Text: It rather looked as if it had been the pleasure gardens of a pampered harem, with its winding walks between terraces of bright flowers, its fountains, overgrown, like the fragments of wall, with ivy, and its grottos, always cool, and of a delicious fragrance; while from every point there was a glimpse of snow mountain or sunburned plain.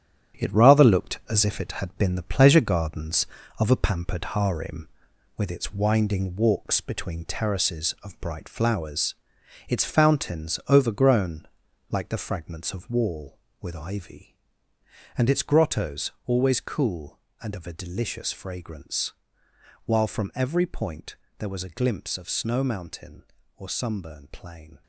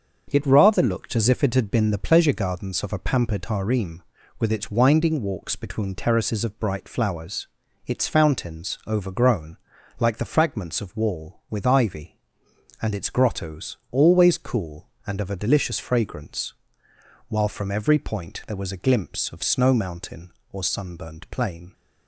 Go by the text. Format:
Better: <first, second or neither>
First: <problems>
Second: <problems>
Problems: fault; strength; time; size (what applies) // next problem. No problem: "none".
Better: second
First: gets quieter; strong; throughout; 7 dB // starts louder than the rest; strong; until 1.4 s; 8.5 dB // pauses between "point" and "there"; slight; at 21.1 s; 0.22 s long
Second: starts louder than the rest; until 1.3 s; 6.5 dB